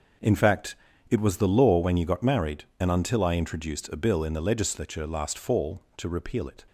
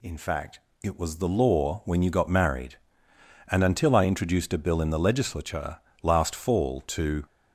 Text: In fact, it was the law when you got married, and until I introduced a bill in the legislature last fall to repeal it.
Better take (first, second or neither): first